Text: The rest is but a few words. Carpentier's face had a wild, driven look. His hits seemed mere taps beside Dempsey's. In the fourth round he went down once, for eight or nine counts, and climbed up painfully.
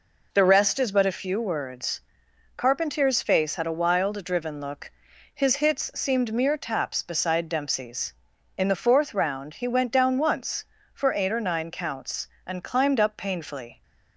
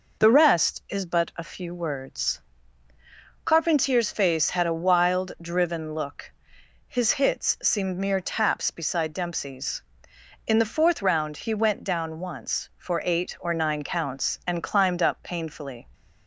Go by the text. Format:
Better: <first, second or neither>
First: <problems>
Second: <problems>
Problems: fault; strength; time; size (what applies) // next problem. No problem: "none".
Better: neither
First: none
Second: none